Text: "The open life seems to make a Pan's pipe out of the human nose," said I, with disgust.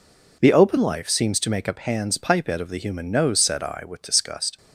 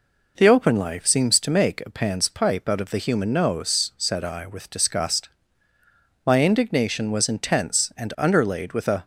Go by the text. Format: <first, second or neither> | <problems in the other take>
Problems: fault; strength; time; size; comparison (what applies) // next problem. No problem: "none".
first | goes on to say "My indignation was intense and underlaid with a"; strong; from 6.2 s on; 2.7 s long